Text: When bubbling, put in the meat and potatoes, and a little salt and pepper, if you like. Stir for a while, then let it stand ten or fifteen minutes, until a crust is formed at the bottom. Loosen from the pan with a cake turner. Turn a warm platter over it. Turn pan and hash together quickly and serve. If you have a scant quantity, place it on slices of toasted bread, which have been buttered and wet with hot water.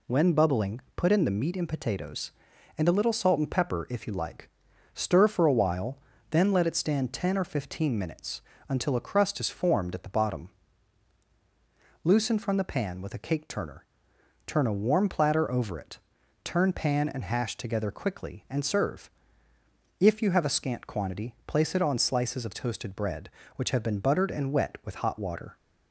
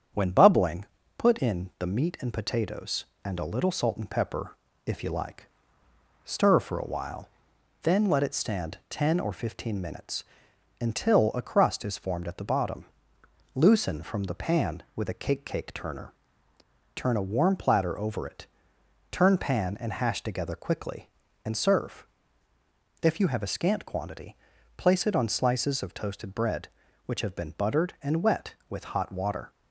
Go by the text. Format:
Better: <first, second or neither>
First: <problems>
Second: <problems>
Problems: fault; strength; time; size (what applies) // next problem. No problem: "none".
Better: first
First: none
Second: starts louder than the rest; strong; until 1.4 s; 8 dB // says "cake" twice; at 15.4 s